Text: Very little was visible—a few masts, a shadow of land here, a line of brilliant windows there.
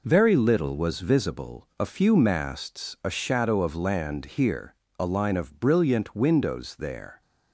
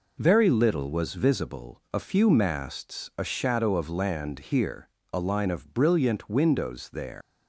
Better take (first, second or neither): first